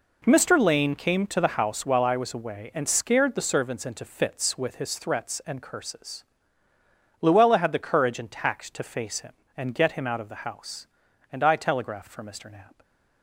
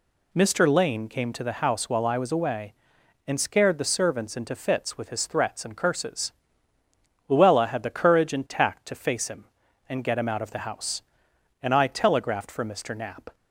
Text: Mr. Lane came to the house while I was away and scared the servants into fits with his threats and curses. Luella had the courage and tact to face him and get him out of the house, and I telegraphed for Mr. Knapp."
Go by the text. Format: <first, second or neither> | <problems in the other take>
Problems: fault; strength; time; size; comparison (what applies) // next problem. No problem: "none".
neither | none